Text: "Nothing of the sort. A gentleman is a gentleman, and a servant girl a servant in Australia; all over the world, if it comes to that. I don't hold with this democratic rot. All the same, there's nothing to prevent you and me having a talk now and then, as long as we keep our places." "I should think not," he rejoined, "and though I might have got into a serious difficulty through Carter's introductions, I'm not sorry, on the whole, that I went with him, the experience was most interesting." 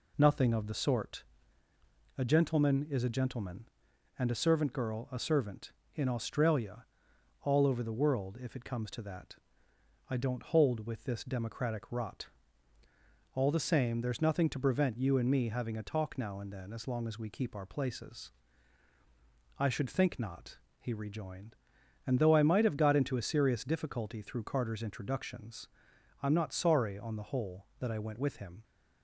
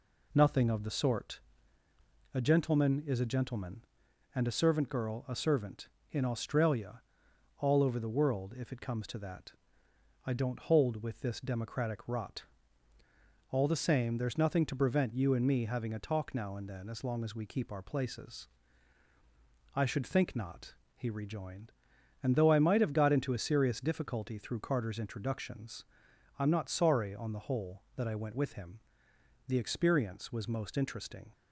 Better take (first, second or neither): second